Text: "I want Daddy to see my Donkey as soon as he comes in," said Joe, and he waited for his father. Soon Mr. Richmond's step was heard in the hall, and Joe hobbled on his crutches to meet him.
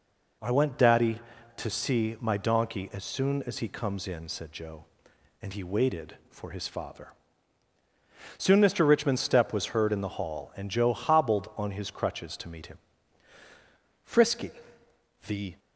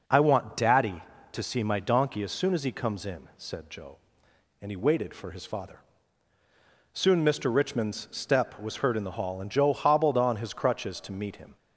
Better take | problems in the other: second | goes on to say "Frisky the"; from 14.0 s on; 1.5 s long

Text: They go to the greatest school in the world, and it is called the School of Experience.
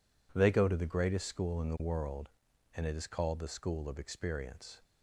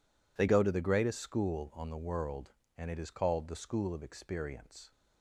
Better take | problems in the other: first | says "on" for "in"; at 1.7 s

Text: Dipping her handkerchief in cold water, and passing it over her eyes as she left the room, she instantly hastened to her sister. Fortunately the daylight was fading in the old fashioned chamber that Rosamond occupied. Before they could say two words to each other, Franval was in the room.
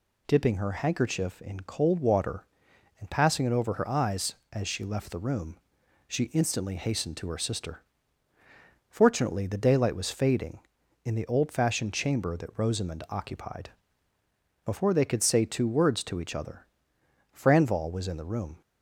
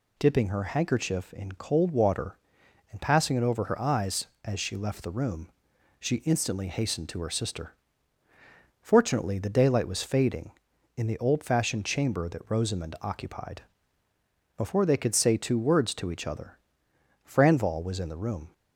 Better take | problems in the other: neither | none

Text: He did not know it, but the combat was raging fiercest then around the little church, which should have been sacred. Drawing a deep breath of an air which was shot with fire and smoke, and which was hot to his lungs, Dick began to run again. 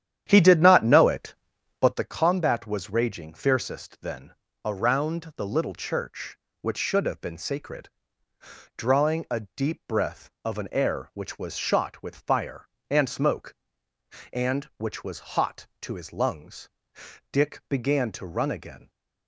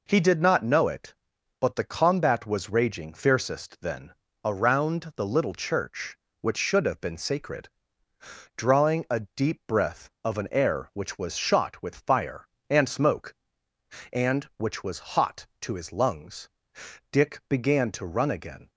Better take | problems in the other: second | starts louder than the rest; strong; until 2.0 s; 10 dB // pauses between "then" and "around"; slight; at 4.3 s; 0.32 s long; slight in the second

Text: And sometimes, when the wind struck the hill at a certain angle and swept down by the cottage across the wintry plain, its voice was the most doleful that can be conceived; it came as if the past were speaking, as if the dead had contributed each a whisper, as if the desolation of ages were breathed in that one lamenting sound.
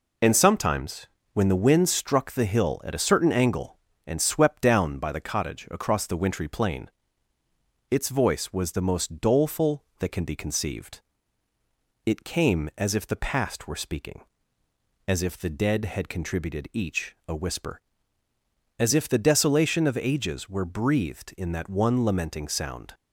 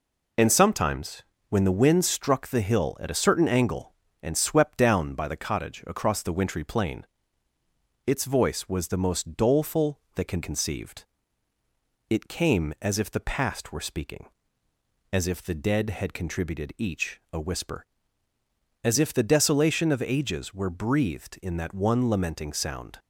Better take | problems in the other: first | skips "be"; at 10.4 s

